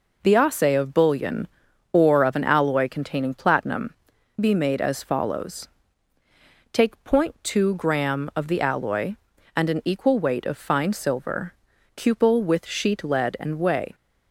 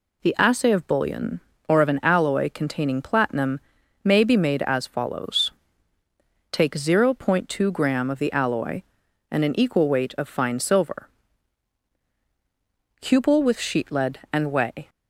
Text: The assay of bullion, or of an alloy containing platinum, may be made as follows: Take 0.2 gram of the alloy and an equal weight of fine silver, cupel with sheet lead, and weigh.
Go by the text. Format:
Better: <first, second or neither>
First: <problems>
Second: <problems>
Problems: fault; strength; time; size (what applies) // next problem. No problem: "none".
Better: second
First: skips "may"; at 4.1 s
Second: none